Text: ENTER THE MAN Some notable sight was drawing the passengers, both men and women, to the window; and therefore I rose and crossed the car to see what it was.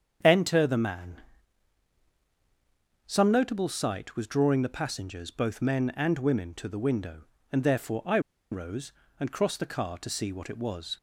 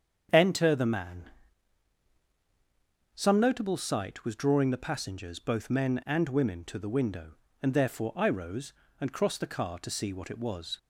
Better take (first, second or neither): second